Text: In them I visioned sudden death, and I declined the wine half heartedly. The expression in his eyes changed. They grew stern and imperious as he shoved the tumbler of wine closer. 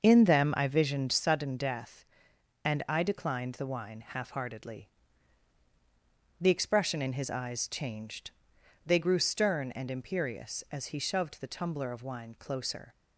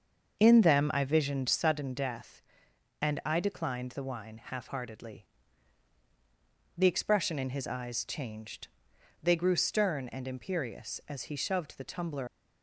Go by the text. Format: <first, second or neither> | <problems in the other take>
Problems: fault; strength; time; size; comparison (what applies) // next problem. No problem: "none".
first | starts louder than the rest; until 1.4 s; 6.5 dB; also in the first // stops before "of wine closer"; at 12.2 s